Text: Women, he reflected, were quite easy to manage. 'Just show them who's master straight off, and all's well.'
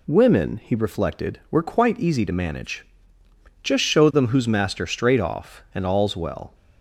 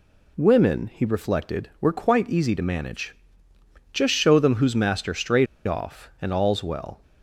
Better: first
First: none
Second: pauses between "straight" and "off"; slight; at 5.4 s; 0.21 s long

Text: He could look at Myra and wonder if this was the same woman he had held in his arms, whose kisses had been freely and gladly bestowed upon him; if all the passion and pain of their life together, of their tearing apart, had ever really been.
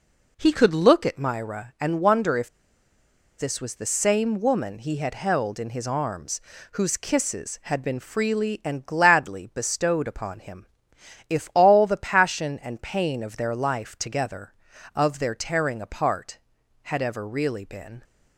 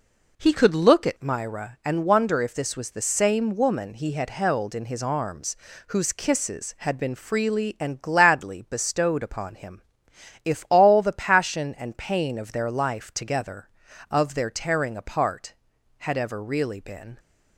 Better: second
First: pauses between "if" and "this"; noticeable; at 2.4 s; 0.90 s long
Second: none

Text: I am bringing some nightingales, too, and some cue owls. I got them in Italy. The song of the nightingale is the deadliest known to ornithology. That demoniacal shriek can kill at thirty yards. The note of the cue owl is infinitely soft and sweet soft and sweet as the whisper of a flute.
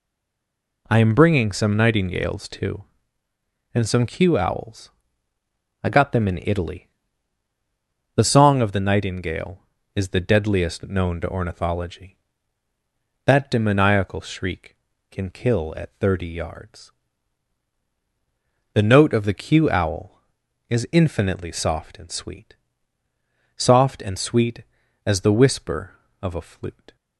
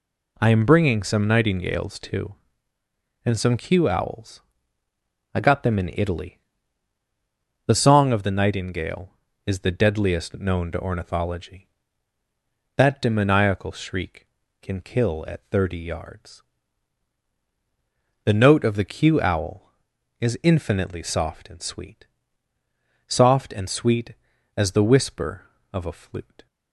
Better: second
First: stays silent before the first word; slight; until 0.8 s; 0.8 s long // pauses between "sweet" and "soft"; at 22.5 s; 1.0 s long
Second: pauses between "sweet" and "soft"; at 22.0 s; 1.0 s long

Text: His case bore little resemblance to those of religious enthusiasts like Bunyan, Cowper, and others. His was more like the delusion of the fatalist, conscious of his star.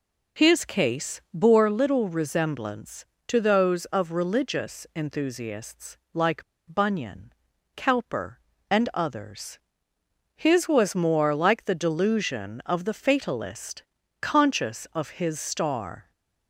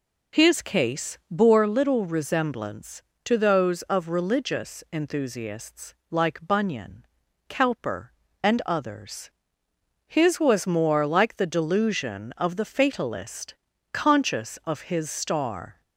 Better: second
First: pauses between "enthusiasts" and "like"; slight; at 5.9 s; 0.16 s long // pauses between "like" and "Bunyan"; slight; at 6.4 s; 0.26 s long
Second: pauses between "enthusiasts" and "like"; slight; at 5.9 s; 0.16 s long

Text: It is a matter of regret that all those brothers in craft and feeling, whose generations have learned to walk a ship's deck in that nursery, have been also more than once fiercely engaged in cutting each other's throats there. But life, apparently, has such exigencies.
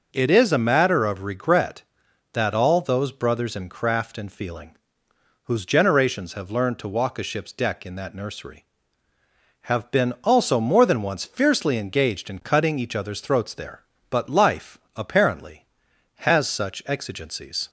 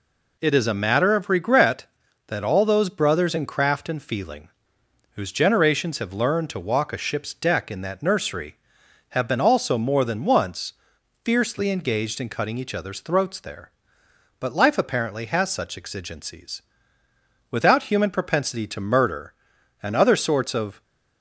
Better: first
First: none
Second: pauses between "once" and "fiercely"; noticeable; at 10.7 s; 0.50 s long // goes on to say "Without human propensity to murder and other sorts of"; strong; from 17.4 s on; 3.3 s long

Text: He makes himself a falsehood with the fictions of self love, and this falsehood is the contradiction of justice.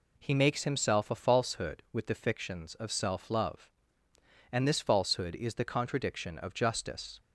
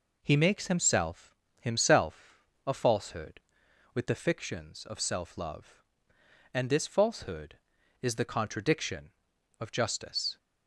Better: first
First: none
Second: says "himself" twice; at 1.5 s

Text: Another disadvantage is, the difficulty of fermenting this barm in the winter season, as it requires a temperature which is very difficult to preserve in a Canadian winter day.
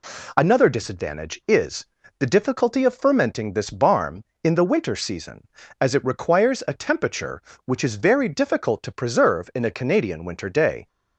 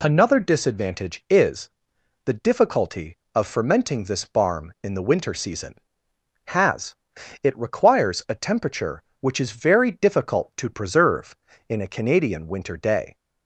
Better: first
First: none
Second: says "has" for "as"; at 6.4 s

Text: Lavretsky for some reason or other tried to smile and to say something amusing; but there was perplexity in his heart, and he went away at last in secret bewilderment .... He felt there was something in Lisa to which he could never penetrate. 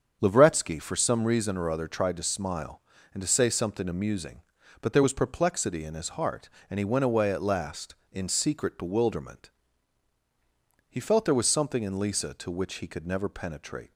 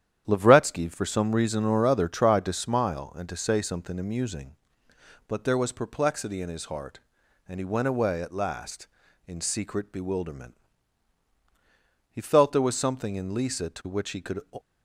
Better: first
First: starts louder than the rest; strong; until 1.2 s; 7 dB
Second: starts louder than the rest; strong; until 1.2 s; 10 dB // stops before "never penetrate"; at 14.5 s

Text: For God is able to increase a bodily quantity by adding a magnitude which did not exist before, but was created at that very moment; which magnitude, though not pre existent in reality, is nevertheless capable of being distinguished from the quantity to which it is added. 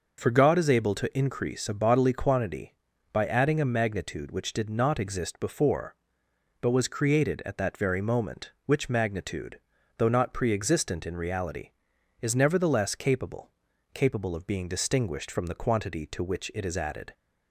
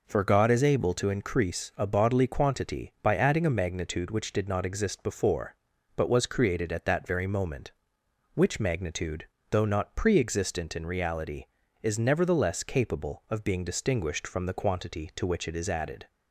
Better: second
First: says "capable" twice; at 13.9 s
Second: none

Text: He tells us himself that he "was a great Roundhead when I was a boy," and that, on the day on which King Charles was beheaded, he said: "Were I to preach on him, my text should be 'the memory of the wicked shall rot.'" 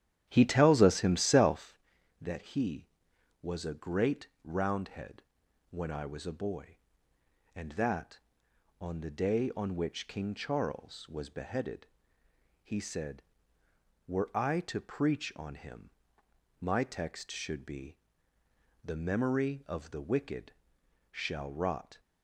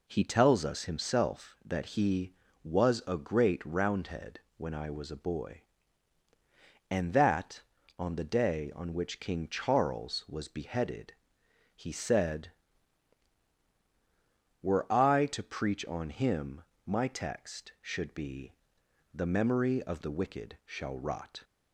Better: second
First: starts louder than the rest; strong; until 1.8 s; 11 dB // pauses between "great" and "Roundhead"; slight; at 4.2 s; 0.16 s long // pauses between "Roundhead" and "when"; noticeable; at 5.2 s; 0.48 s long // pauses between "be" and "the"; noticeable; at 17.9 s; 0.88 s long // pauses between "wicked" and "shall"; noticeable; at 20.5 s; 0.58 s long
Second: pauses between "Roundhead" and "when"; slight; at 4.3 s; 0.16 s long // pauses between "be" and "the"; noticeable; at 18.5 s; 0.60 s long

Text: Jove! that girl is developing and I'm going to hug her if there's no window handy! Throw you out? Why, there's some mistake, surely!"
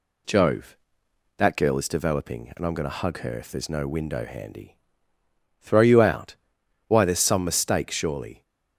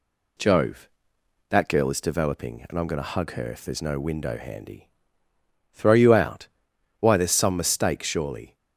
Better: neither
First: none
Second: none

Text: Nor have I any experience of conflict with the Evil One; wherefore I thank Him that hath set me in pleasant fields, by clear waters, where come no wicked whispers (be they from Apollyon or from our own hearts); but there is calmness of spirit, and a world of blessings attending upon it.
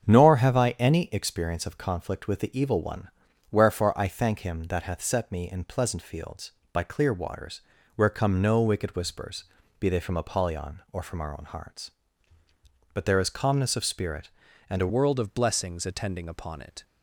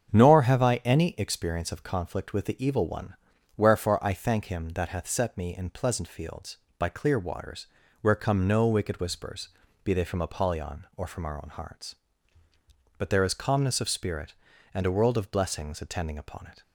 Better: second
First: starts louder than the rest; strong; until 1.0 s; 7.5 dB // changes voice at "world"; from 14.8 s on; 2.0 s long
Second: starts louder than the rest; strong; until 1.1 s; 7.5 dB

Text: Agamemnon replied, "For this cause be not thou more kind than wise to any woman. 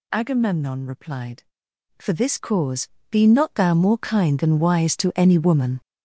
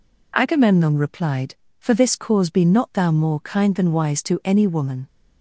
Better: second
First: gets louder; strong; throughout; 9.5 dB // pauses between "cause" and "be"; slight; at 2.8 s; 0.24 s long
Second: none

